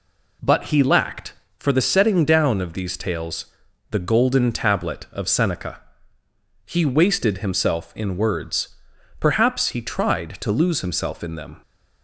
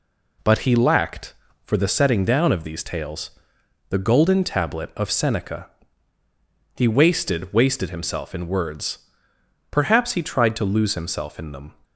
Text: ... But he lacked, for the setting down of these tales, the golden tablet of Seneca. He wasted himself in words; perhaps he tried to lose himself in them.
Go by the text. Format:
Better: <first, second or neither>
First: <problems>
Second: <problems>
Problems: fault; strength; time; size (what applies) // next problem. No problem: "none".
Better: first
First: none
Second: says "wasted" twice; at 7.5 s